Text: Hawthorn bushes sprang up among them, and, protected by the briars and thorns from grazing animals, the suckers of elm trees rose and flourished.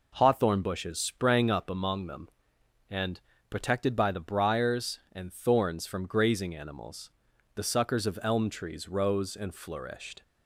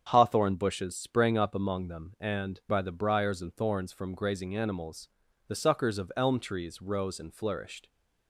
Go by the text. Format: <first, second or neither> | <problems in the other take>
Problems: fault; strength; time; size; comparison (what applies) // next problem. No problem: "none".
first | starts louder than the rest; strong; until 1.0 s; 7.5 dB // skips "protected"; at 2.6 s